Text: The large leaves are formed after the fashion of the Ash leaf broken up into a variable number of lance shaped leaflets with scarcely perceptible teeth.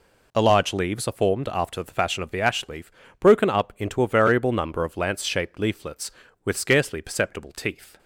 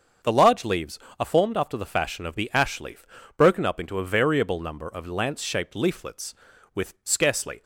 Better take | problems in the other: first | starts louder than the rest; until 1.4 s; 7 dB // pauses between "leaf" and "broken"; slight; at 3.0 s; 0.30 s long; slight in the first // stops before "perceptible teeth"; at 7.6 s

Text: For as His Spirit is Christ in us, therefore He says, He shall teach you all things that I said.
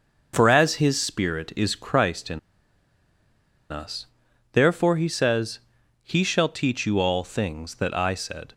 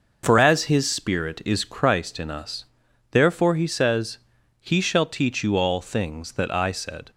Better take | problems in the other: second | pauses between "in" and "us"; strong; at 2.3 s; 1.3 s long

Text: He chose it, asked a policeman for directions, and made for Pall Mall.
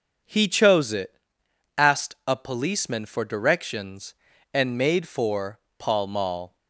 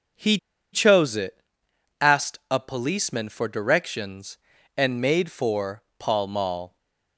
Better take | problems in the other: first | starts louder than the rest; until 2.0 s; 6 dB // pauses between "He" and "chose"; slight; at 0.3 s; 0.36 s long // pauses between "for" and "Pall"; slight; at 5.8 s; 0.16 s long; slight in the first

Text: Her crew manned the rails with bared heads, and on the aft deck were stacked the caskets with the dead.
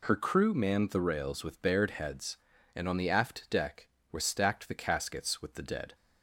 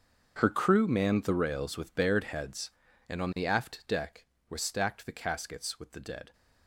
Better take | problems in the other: first | gets quieter; strong; throughout; 17 dB

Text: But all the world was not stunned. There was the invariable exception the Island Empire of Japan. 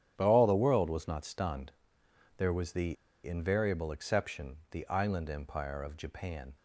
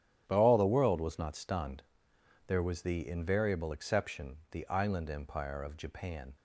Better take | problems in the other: second | starts louder than the rest; strong; until 1.1 s; 9.5 dB; strong in the second // pauses between "the" and "invariable"; slight; at 2.9 s; 0.30 s long

